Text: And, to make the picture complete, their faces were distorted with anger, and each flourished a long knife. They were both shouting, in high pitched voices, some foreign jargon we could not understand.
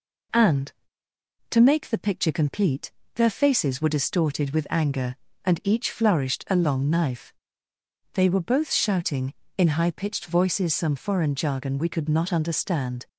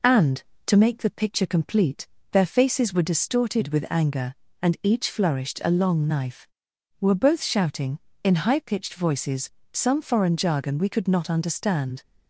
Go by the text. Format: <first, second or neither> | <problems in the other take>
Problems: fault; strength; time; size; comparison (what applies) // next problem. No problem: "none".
first | skips "They"; at 6.7 s